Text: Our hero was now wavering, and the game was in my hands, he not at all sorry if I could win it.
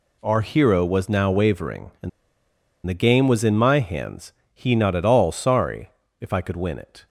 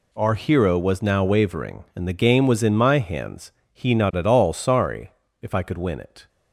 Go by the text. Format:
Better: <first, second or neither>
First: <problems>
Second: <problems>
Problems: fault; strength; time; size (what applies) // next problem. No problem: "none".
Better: second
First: pauses between "and" and "the"; noticeable; at 2.0 s; 0.76 s long // pauses between "sorry" and "if"; slight; at 5.8 s; 0.32 s long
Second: pauses between "sorry" and "if"; slight; at 5.0 s; 0.32 s long